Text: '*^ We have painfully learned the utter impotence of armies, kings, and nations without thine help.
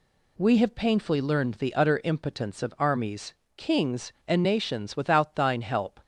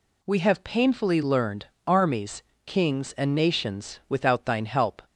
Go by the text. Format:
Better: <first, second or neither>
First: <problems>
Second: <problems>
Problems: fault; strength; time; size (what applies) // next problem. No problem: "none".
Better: first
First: none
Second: skips "the utter impotence of"; at 1.7 s